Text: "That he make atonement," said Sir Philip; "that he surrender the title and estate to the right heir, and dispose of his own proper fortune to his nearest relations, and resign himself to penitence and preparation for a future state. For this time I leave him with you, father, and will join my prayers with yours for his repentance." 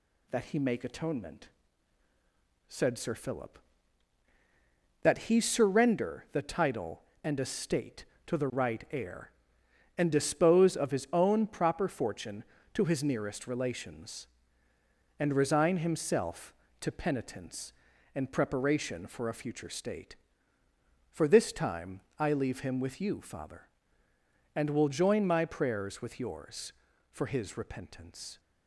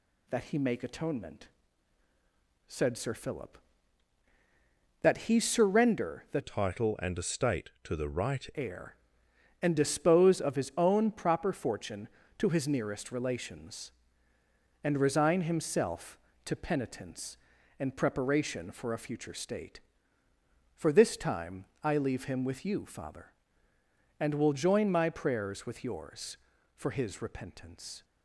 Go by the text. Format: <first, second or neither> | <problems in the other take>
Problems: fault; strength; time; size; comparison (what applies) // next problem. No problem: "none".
first | changes voice from "title" to "right"; from 6.4 to 8.4 s; 2.0 s long // pauses between "time" and "I"; slight; at 21.6 s; 0.18 s long; slight in the first